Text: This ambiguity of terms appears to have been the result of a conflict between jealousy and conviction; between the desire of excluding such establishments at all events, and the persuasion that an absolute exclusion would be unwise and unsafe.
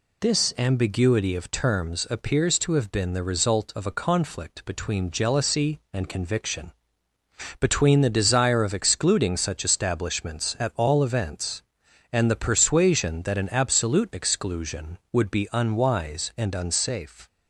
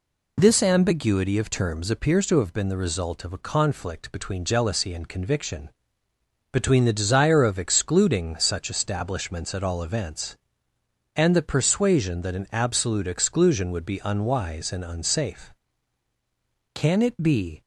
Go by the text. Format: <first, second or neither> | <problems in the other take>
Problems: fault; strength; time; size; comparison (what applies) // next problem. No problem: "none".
first | goes on to say "Can it be"; noticeable; from 16.7 s on; 0.88 s long